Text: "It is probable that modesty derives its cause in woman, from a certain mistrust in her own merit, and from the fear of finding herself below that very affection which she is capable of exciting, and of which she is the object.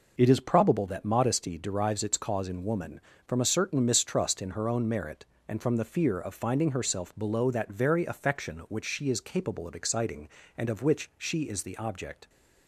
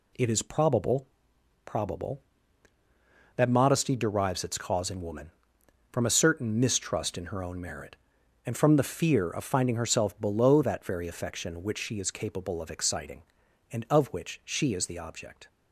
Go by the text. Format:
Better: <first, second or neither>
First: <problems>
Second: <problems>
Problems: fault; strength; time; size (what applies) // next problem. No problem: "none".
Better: first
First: none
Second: says "probable" twice; at 1.6 s